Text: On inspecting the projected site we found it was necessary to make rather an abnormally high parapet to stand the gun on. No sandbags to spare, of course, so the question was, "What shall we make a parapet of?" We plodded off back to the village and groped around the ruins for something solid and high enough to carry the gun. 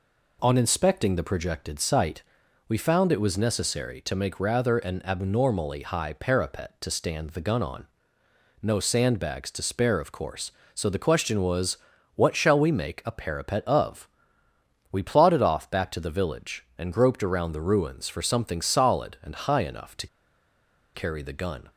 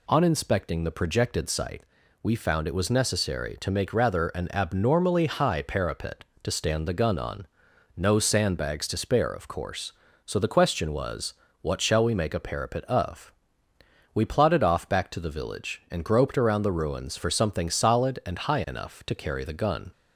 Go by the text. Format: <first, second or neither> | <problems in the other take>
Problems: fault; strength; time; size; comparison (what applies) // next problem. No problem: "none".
second | pauses between "site" and "we"; at 2.2 s; 0.44 s long; also in the second // pauses between "to" and "carry"; noticeable; at 20.0 s; 0.88 s long